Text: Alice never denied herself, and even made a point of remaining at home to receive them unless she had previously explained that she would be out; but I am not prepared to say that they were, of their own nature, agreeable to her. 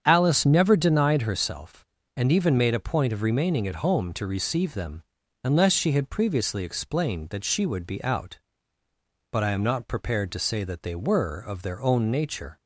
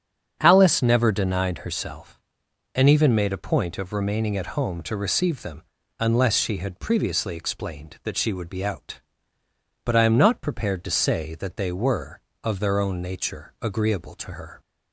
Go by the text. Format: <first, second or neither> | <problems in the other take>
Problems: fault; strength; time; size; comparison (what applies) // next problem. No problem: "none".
second | starts louder than the rest; strong; until 1.0 s; 8 dB; strong in the second // pauses between "them" and "unless"; at 5.0 s; 0.42 s long; slight in the second // stops before "agreeable to her"; at 12.6 s